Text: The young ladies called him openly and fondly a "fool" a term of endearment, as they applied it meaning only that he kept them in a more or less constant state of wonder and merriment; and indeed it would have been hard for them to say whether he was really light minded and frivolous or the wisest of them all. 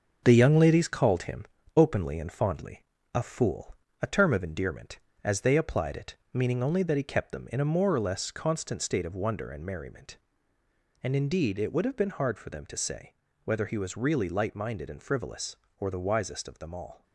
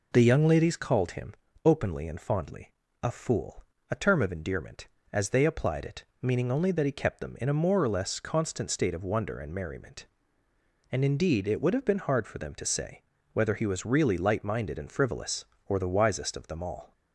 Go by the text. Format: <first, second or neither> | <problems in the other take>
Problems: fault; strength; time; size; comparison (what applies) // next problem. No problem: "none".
second | gets quieter; throughout; 7 dB // pauses between "him" and "openly"; slight; at 1.4 s; 0.32 s long; slight in the second // pauses between "fondly" and "a"; slight; at 2.8 s; 0.32 s long; slight in the second // pauses between "fool" and "a"; slight; at 3.7 s; 0.26 s long; slight in the second // pauses between "it" and "meaning"; slight; at 6.1 s; 0.18 s long; slight in the second // pauses between "say" and "whether"; slight; at 13.1 s; 0.28 s long; slight in the second